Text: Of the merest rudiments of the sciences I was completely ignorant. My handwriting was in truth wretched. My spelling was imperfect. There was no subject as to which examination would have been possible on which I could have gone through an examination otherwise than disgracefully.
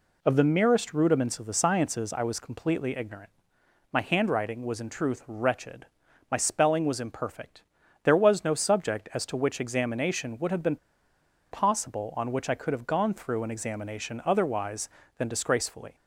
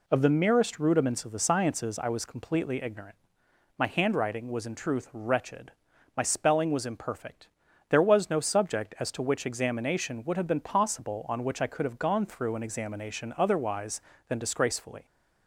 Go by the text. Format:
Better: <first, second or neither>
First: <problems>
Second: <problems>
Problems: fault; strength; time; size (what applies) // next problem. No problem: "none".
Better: second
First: pauses between "been" and "possible"; noticeable; at 10.7 s; 0.75 s long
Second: none